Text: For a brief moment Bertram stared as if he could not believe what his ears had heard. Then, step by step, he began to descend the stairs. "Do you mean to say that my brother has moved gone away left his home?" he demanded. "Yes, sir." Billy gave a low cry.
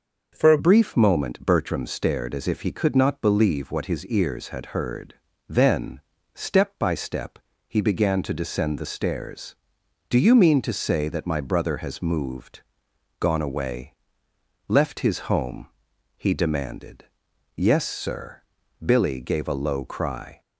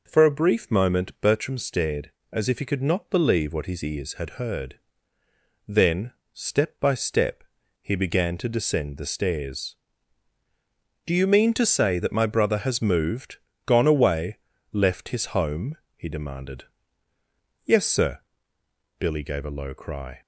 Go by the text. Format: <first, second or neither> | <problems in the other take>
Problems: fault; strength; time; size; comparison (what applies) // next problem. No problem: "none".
second | changes voice at "brief"; from 0.5 s on; 19.9 s long // pauses between "moved" and "gone"; noticeable; at 12.6 s; 0.56 s long; slight in the second // pauses between "away" and "left"; noticeable; at 13.9 s; 0.76 s long; slight in the second